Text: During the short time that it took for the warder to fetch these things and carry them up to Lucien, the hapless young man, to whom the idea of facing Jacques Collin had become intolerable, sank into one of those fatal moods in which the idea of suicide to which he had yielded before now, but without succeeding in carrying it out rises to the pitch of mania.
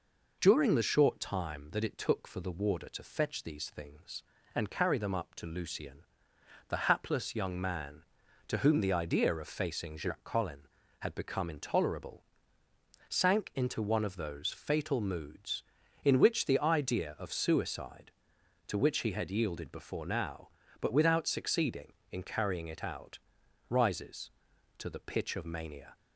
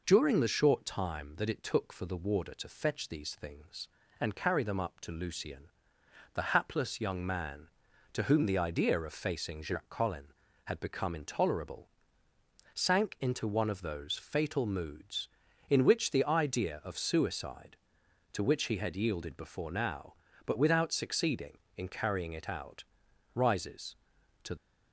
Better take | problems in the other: first | pauses between "out" and "rises"; noticeable; at 22.8 s; 0.52 s long; noticeable in the first // stops before "the pitch of mania"; at 24.5 s

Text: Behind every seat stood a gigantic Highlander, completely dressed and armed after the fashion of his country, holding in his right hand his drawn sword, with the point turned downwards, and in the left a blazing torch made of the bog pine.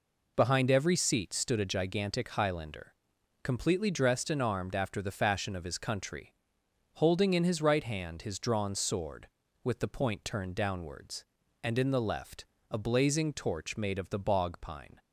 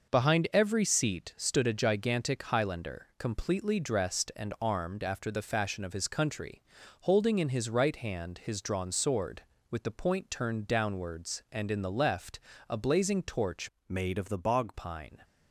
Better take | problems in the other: first | pauses between "left" and "a"; slight; at 12.3 s; 0.30 s long; slight in the first // changes voice from "made" to "bog"; from 13.8 to 14.7 s; 0.9 s long

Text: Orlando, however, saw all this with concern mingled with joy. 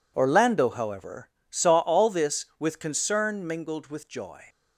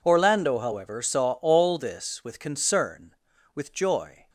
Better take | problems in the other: first | skips "mingled"; at 3.3 s

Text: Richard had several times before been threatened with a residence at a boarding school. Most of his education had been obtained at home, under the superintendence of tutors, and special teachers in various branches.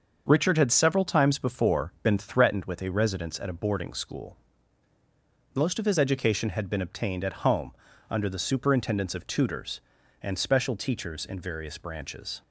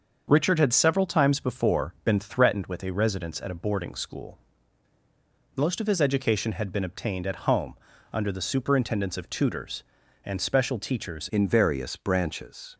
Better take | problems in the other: first | starts louder than the rest; until 1.2 s; 6.5 dB; also in the first // changes voice at "in"; from 11.3 s on; 1.4 s long

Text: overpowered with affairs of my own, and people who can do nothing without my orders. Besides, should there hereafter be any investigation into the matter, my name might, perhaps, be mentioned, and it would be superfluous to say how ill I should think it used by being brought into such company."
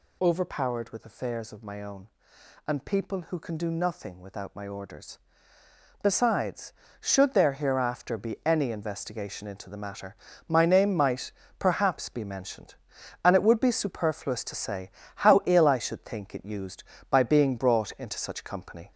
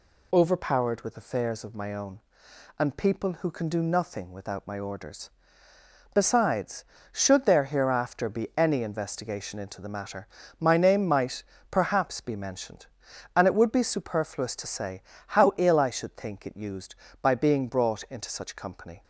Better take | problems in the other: second | gets louder; throughout; 3.5 dB // pauses between "say" and "how"; slight; at 14.8 s; 0.26 s long; slight in the second

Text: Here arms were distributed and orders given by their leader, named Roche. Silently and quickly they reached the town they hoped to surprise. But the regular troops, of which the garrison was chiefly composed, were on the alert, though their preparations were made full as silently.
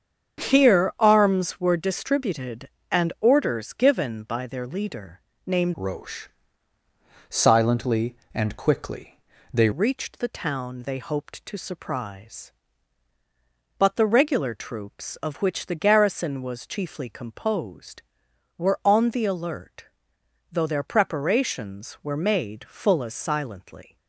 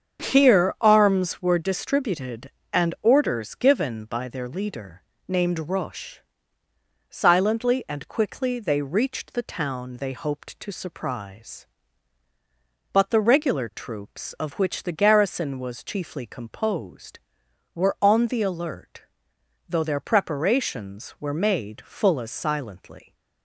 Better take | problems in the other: second | starts louder than the rest; strong; until 1.4 s; 7.5 dB; strong in the second // changes voice from "Roche" to "they"; from 5.7 to 9.6 s; 3.9 s long // pauses between "quickly" and "they"; slight; at 9.1 s; 0.34 s long

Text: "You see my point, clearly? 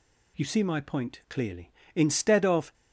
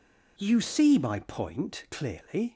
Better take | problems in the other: second | goes on to say "Instead of"; noticeable; from 1.9 s on; 0.78 s long

